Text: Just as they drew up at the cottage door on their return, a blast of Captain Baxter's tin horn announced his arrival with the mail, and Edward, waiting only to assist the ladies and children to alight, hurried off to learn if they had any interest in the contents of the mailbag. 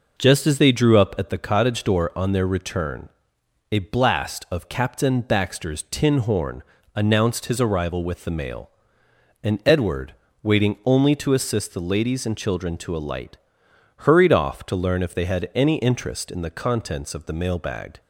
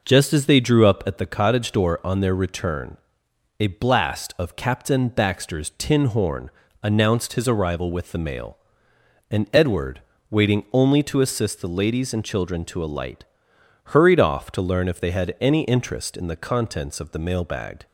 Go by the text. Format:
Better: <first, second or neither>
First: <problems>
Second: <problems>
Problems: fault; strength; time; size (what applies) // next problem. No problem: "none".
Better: neither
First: pauses between "horn" and "announced"; slight; at 6.6 s; 0.32 s long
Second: pauses between "horn" and "announced"; slight; at 6.4 s; 0.32 s long